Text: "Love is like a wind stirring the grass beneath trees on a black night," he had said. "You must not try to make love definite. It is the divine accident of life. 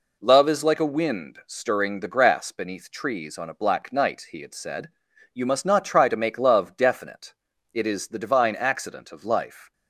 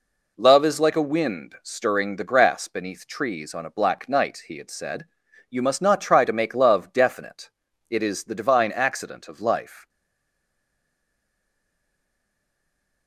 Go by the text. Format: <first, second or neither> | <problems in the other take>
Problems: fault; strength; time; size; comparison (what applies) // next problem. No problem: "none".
first | stays silent after the last word; strong; from 9.8 s on; 3.2 s long